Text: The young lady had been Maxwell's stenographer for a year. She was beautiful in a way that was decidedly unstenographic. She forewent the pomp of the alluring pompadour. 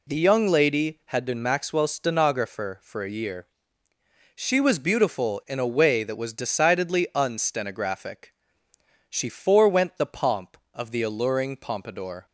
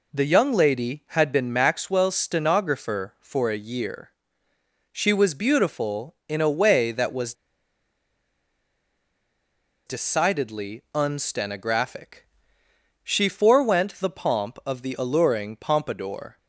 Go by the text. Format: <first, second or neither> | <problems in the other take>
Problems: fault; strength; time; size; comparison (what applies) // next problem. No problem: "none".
first | pauses between "was" and "decidedly"; strong; at 7.3 s; 2.5 s long